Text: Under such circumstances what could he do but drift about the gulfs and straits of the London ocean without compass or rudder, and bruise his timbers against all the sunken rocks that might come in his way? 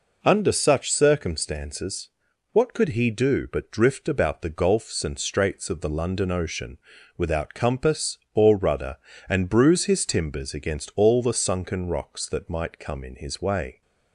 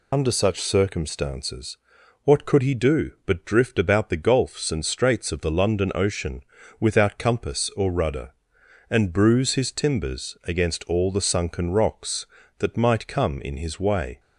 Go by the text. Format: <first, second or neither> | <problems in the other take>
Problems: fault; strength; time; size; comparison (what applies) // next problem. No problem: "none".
first | loses the start of "Under"; at 0.1 s; 65 ms // pauses between "circumstances" and "what"; noticeable; at 1.7 s; 0.46 s long; also in the first // pauses between "ocean" and "without"; at 6.4 s; 0.38 s long; also in the first